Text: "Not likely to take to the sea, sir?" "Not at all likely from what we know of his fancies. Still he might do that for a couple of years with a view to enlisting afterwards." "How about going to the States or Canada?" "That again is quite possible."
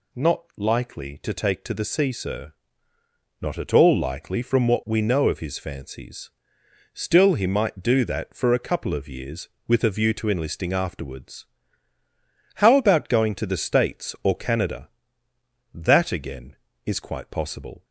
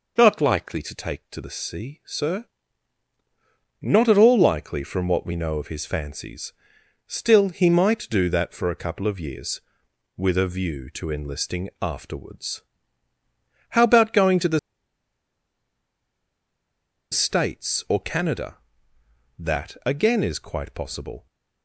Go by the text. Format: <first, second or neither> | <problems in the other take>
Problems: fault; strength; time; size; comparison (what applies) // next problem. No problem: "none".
first | pauses between "the" and "States"; strong; at 14.5 s; 2.5 s long